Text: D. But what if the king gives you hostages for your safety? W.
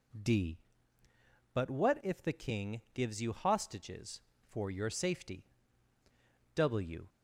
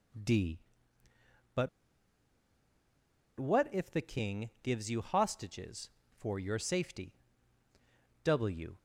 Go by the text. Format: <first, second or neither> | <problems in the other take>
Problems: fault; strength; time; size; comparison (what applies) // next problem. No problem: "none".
first | pauses between "But" and "what"; strong; at 1.6 s; 1.7 s long